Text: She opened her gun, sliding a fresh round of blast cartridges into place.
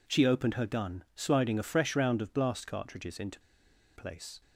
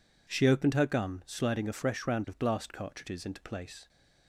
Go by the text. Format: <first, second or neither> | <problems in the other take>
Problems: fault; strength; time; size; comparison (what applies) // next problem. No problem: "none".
second | pauses between "into" and "place"; noticeable; at 3.3 s; 0.55 s long